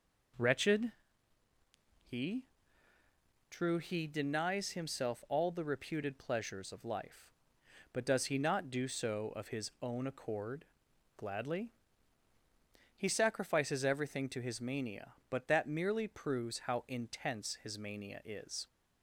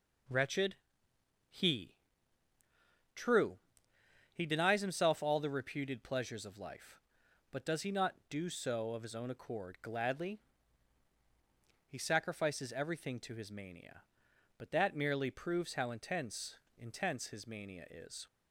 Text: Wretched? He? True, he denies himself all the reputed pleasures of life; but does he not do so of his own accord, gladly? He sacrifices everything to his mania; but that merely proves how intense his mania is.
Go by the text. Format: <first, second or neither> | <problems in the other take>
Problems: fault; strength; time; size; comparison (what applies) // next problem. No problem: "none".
first | says "intense" twice; at 16.7 s